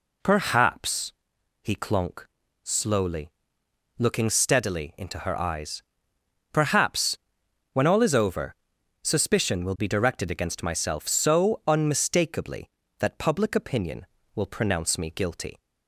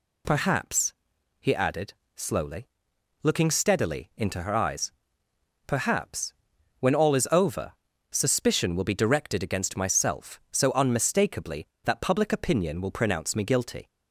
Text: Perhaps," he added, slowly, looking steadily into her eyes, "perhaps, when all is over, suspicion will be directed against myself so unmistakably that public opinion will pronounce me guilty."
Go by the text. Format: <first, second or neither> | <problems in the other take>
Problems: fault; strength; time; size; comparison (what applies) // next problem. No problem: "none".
second | says "clonk" for "added"; at 1.7 s